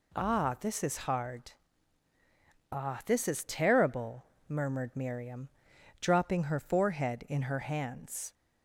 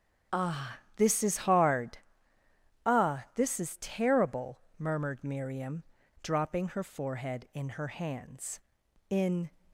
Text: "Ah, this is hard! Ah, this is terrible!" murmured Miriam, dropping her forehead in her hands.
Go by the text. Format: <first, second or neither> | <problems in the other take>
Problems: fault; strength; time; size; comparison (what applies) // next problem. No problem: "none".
first | starts louder than the rest; strong; until 1.5 s; 7 dB // goes on to say "In"; slight; from 9.0 s on; 0.40 s long